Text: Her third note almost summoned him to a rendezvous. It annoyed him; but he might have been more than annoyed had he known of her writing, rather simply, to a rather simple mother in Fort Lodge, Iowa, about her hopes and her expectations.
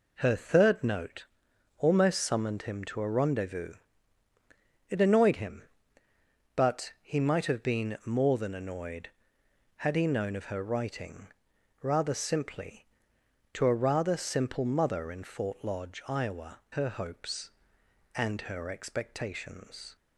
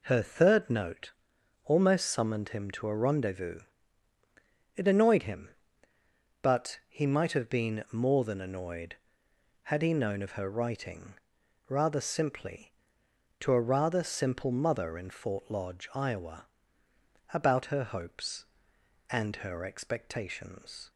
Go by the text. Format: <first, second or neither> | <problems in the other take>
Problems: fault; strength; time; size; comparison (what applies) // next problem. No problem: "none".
second | pauses between "note" and "almost"; noticeable; at 1.2 s; 0.50 s long; noticeable in the second // skips "about"; at 16.6 s